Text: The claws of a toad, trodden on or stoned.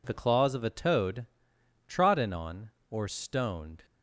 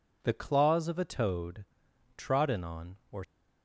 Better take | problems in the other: first | stops before "stoned"; at 3.2 s

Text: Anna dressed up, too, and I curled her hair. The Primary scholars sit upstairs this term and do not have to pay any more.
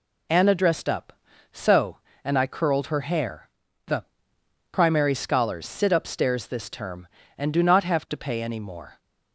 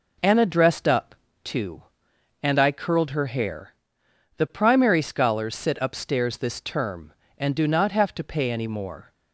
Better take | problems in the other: second | says "so" for "too"; at 1.5 s // pauses between "The" and "Primary"; noticeable; at 4.0 s; 0.68 s long

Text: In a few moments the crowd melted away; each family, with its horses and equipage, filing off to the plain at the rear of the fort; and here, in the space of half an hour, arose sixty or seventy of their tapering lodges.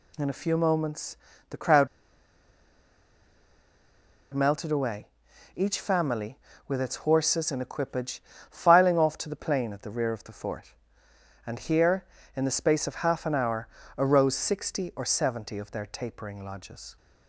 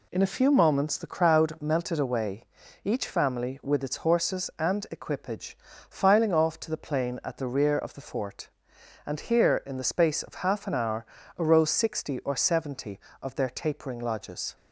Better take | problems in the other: second | pauses between "moments" and "the"; slight; at 1.1 s; 0.32 s long // pauses between "crowd" and "melted"; strong; at 1.8 s; 2.4 s long

